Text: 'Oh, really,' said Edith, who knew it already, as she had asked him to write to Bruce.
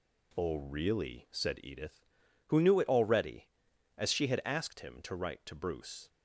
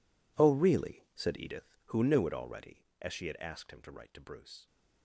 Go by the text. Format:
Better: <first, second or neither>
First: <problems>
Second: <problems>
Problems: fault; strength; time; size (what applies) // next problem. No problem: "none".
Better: first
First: none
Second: gets quieter; strong; throughout; 16 dB